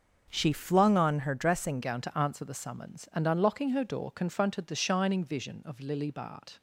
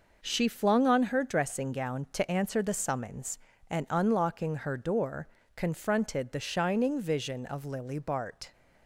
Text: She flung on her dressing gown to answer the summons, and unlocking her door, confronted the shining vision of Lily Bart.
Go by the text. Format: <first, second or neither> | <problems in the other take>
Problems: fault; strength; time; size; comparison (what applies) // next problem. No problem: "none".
second | starts louder than the rest; until 1.2 s; 6 dB // changes voice at "gown"; from 1.8 s on; 4.8 s long